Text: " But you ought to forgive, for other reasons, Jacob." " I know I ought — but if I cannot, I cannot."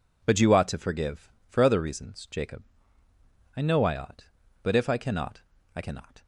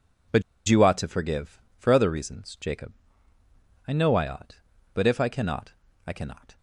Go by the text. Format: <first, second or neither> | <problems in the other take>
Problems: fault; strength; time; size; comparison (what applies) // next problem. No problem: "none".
first | pauses between "But" and "you"; slight; at 0.4 s; 0.26 s long